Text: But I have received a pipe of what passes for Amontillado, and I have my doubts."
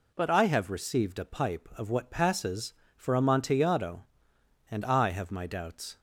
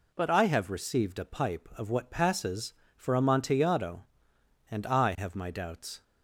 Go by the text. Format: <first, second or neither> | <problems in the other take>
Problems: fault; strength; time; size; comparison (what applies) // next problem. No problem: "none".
neither | none